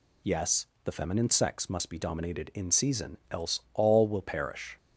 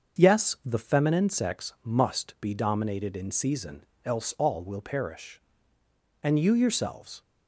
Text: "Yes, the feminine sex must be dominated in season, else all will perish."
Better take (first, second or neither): first